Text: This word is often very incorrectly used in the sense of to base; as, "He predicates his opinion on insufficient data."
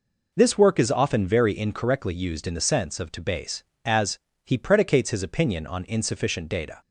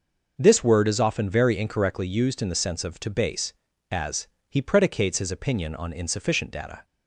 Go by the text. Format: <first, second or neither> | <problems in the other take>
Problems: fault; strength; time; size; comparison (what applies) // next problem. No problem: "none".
second | says "work" for "word"; at 0.5 s